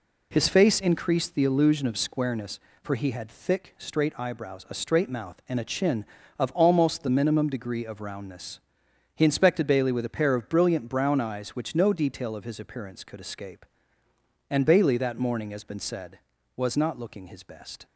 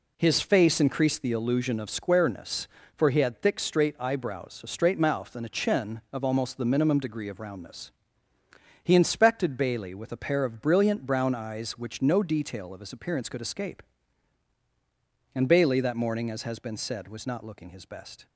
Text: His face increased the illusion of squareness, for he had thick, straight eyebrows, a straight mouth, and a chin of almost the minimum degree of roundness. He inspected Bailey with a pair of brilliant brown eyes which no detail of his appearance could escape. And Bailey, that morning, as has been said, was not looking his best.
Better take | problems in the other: second | skips "has"; at 15.6 s

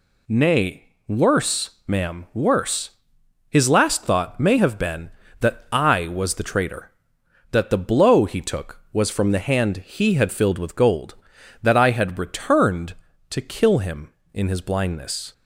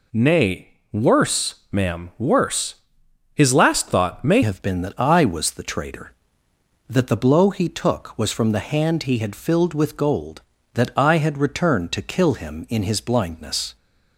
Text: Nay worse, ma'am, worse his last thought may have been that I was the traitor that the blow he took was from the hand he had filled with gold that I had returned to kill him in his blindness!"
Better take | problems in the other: first | pauses between "worse" and "his"; noticeable; at 2.7 s; 0.58 s long; noticeable in the first // changes voice at "have"; from 4.4 s on; 9.3 s long

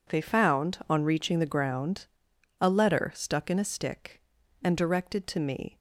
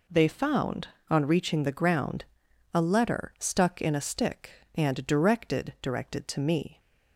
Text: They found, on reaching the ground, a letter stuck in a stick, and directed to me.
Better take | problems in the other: first | says "directed" twice; at 5.8 s

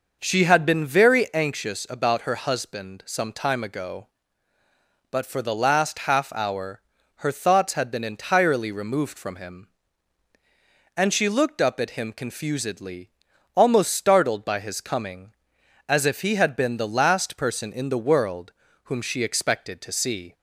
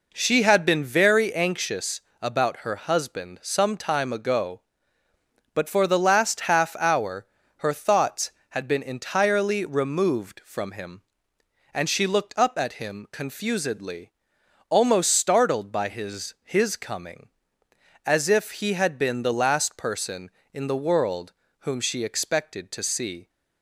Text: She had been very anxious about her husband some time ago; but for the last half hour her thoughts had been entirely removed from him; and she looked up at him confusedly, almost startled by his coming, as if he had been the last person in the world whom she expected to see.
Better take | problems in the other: first | pauses between "anxious" and "about"; slight; at 2.0 s; 0.18 s long // pauses between "hour" and "her"; slight; at 7.2 s; 0.32 s long; also in the first // says "his" twice; at 16.4 s // pauses between "world" and "whom"; slight; at 21.3 s; 0.36 s long; slight in the first

